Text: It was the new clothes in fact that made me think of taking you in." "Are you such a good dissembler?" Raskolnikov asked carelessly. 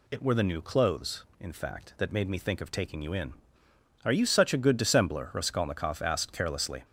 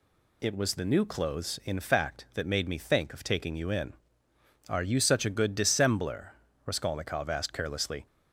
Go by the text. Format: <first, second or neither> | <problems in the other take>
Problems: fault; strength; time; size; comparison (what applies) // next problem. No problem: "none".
second | says "were" for "was"; at 0.2 s